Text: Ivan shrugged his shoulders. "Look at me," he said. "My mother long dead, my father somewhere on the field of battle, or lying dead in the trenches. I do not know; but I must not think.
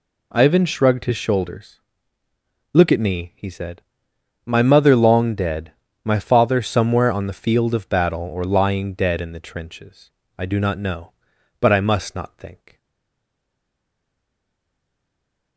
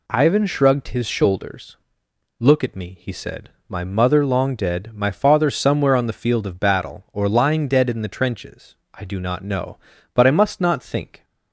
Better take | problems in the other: second | stays silent after the last word; strong; from 12.7 s on; 2.8 s long

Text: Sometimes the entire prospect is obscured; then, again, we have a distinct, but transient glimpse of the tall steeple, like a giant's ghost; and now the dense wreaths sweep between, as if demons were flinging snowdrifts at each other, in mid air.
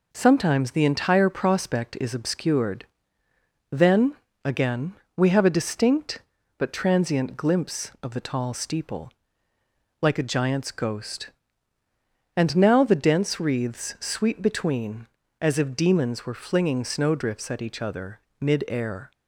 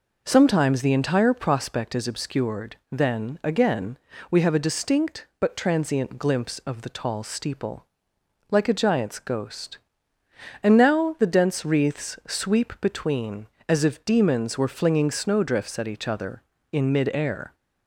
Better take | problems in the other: second | skips "in"; at 18.2 s

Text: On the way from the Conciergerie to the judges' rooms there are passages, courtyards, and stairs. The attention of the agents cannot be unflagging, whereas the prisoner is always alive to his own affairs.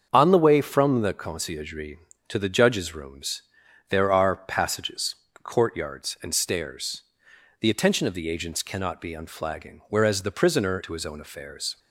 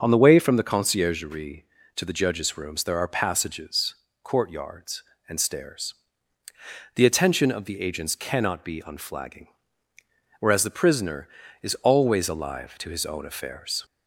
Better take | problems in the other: second | starts louder than the rest; until 1.1 s; 7 dB; also in the second // pauses between "rooms" and "there"; noticeable; at 3.4 s; 0.48 s long // skips "is always alive"; at 10.8 s

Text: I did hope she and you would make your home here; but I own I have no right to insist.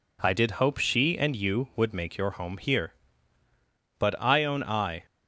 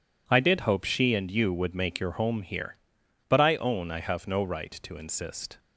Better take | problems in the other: second | stops before "have no right to insist"; at 5.0 s

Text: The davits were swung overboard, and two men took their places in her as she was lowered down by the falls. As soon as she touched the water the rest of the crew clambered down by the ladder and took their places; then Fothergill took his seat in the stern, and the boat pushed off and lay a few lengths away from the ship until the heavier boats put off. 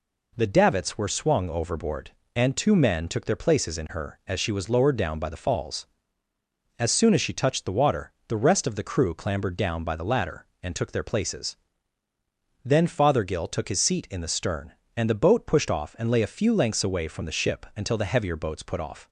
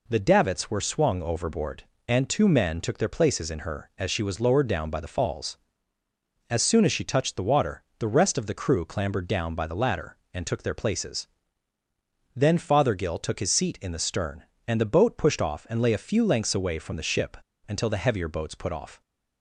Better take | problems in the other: first | pauses between "water" and "the"; slight; at 7.8 s; 0.16 s long; slight in the first // pauses between "ship" and "until"; slight; at 17.3 s; 0.33 s long

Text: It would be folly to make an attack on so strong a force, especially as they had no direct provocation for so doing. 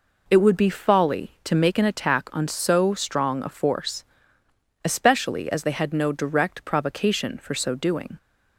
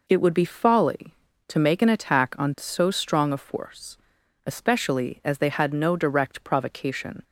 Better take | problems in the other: first | stops before "for so doing"; at 7.2 s

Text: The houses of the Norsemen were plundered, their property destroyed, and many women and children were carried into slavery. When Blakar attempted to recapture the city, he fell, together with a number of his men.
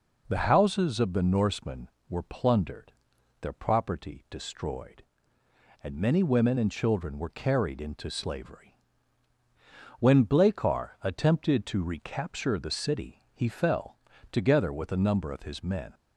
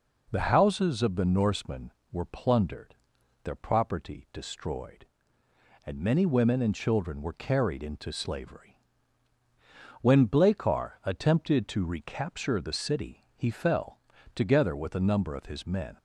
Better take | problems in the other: neither | none

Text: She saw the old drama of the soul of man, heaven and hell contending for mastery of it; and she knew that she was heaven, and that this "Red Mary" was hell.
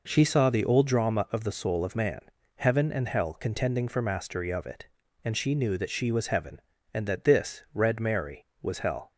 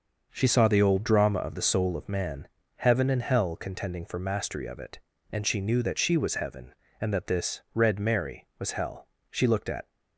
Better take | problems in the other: first | starts louder than the rest; noticeable; until 1.3 s; 6 dB // goes on to say "She looked at"; from 9.2 s on; 0.60 s long

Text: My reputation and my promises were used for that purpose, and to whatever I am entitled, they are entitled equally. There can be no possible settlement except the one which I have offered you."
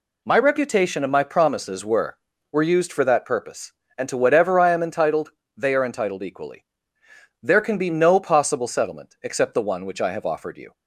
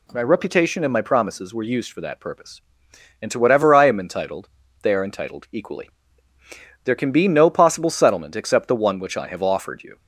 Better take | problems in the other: second | says "were" twice; at 2.5 s

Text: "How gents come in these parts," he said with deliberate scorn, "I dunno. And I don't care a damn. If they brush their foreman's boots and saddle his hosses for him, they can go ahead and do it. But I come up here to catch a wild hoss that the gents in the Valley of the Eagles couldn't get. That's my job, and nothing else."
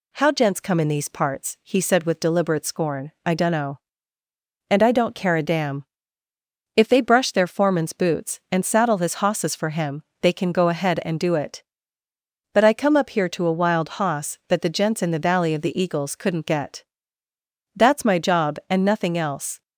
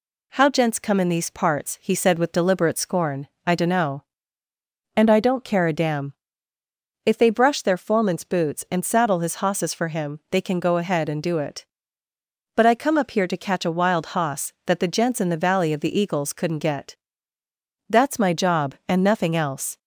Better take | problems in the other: second | skips "catch"; at 13.4 s

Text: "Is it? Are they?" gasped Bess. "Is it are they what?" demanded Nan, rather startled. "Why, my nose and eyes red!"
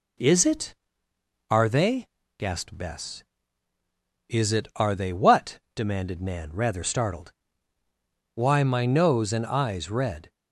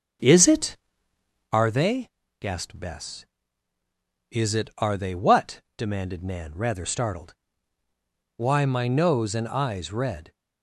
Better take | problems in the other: first | starts louder than the rest; strong; until 1.6 s; 8.5 dB

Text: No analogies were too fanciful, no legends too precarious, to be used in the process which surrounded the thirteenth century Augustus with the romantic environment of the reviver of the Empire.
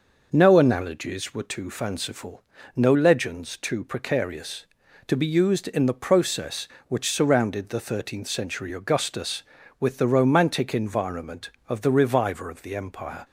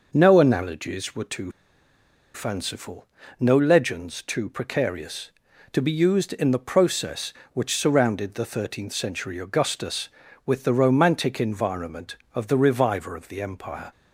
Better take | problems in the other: first | pauses between "too" and "fanciful"; noticeable; at 1.5 s; 0.83 s long

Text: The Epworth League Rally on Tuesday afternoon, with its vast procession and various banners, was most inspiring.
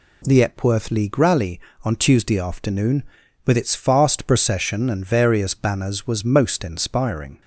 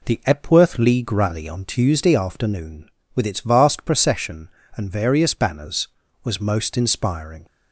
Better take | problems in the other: second | says "fast" for "vast"; at 3.7 s

